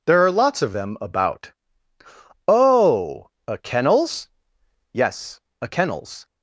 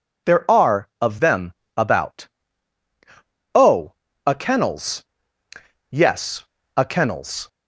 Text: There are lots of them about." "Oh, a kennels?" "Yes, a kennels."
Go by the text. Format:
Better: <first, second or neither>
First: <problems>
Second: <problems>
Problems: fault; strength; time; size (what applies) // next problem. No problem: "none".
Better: first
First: none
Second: skips "lots"; at 0.9 s // pauses between "them" and "about"; slight; at 1.5 s; 0.24 s long